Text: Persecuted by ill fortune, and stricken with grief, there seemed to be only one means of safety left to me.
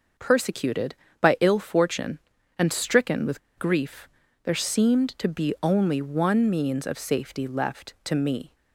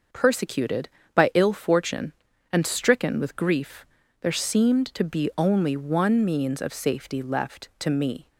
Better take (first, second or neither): second